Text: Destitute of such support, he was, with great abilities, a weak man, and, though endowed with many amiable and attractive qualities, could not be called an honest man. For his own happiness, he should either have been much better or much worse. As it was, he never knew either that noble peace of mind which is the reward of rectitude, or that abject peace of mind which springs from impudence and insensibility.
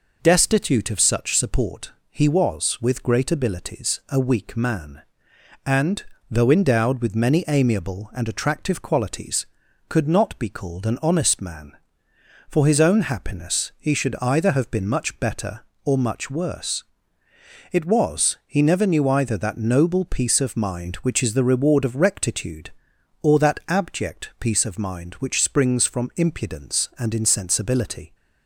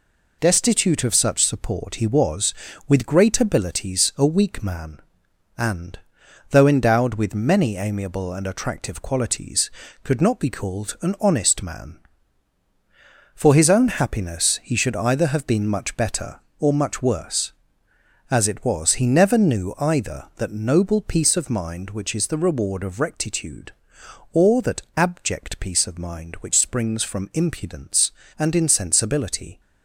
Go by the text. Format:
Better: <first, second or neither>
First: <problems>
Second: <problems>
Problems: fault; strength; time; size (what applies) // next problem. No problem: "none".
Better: second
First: skips "As"; at 17.2 s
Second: none